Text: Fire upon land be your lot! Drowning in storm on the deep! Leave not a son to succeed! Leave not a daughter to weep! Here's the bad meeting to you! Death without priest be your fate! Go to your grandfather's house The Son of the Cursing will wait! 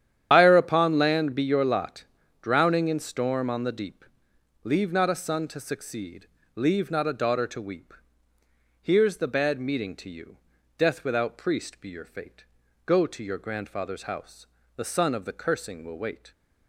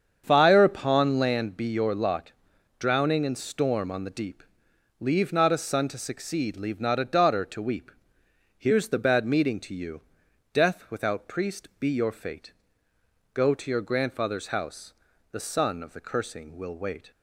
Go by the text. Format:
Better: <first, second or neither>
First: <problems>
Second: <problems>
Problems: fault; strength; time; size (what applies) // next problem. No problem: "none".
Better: second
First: loses the start of "Fire"; at 0.3 s; 80 ms // starts louder than the rest; strong; until 1.3 s; 10 dB // pauses between "house" and "The"; slight; at 14.4 s; 0.30 s long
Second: starts louder than the rest; strong; until 1.2 s; 7.5 dB // pauses between "house" and "The"; slight; at 14.9 s; 0.36 s long